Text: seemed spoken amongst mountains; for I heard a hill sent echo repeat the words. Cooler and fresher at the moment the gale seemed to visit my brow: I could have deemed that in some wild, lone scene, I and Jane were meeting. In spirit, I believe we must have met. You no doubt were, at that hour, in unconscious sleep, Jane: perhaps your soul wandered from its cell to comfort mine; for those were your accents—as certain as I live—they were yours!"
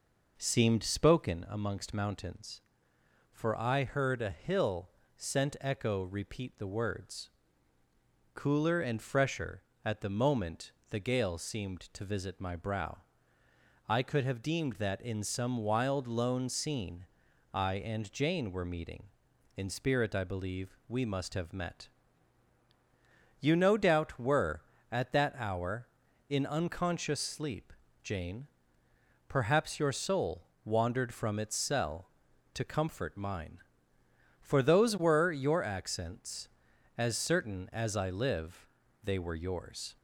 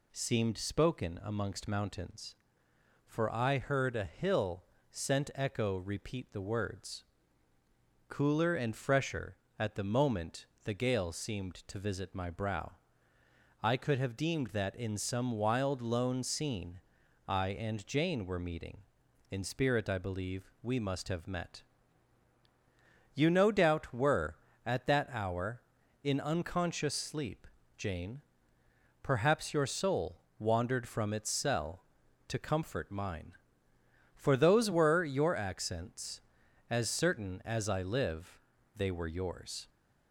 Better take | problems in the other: second | starts louder than the rest; noticeable; until 1.5 s; 5.5 dB // pauses between "hill" and "sent"; slight; at 4.8 s; 0.26 s long; slight in the second // pauses between "moment" and "the"; slight; at 10.7 s; 0.18 s long; slight in the second // pauses between "soul" and "wandered"; slight; at 30.4 s; 0.20 s long; slight in the second

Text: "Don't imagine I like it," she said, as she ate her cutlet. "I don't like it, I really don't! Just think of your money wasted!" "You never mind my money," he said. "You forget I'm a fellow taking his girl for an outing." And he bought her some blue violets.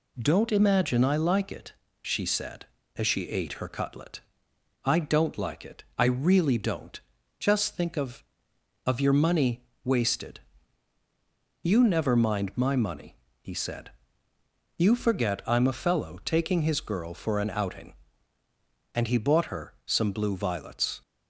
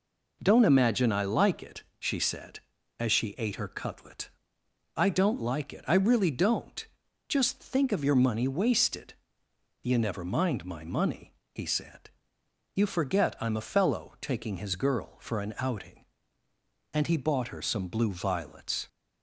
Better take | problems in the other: second | says "of" twice; at 8.8 s // pauses between "money" and "wasted"; slight; at 9.6 s; 0.20 s long

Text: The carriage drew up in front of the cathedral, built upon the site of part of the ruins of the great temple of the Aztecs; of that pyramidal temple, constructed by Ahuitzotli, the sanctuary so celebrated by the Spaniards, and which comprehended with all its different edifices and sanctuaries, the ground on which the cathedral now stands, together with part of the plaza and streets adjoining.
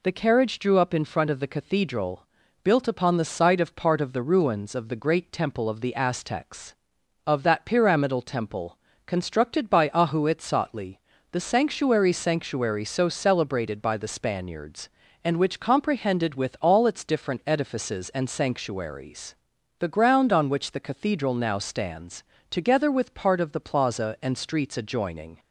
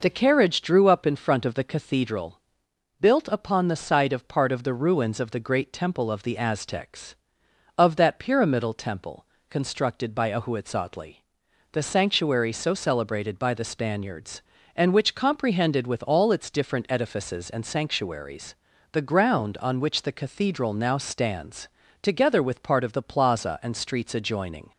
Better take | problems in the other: second | says "sanctuary" twice; at 12.1 s

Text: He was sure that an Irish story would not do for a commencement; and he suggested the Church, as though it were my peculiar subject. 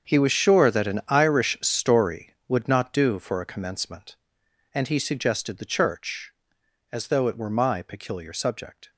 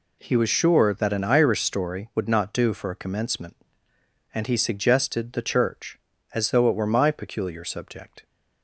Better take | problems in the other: second | gets quieter; strong; throughout; 13.5 dB

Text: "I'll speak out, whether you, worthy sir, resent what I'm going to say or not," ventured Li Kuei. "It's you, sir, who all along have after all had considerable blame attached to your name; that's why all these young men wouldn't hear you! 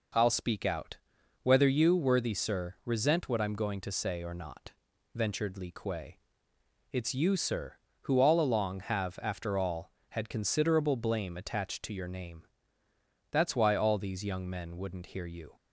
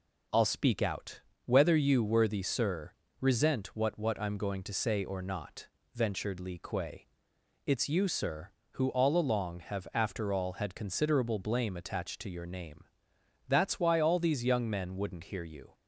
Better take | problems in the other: first | says "what" twice; at 3.9 s

